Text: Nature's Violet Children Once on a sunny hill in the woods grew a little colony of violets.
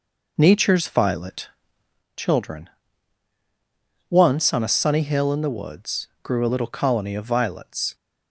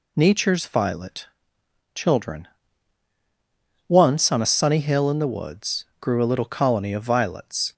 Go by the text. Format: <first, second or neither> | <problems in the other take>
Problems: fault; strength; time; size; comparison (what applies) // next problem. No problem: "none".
second | starts louder than the rest; noticeable; until 2.0 s; 5 dB // pauses between "Violet" and "Children"; noticeable; at 1.4 s; 0.66 s long; noticeable in the second // pauses between "Children" and "Once"; strong; at 2.6 s; 1.4 s long; strong in the second // pauses between "woods" and "grew"; slight; at 6.0 s; 0.16 s long; slight in the second